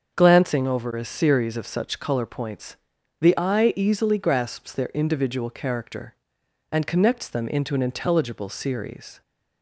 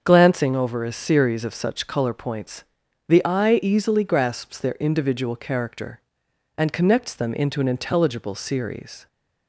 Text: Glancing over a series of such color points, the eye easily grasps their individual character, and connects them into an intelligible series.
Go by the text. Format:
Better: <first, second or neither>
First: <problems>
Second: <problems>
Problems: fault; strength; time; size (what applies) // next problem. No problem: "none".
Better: neither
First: starts louder than the rest; until 1.1 s; 6.5 dB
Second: starts louder than the rest; until 1.0 s; 6.5 dB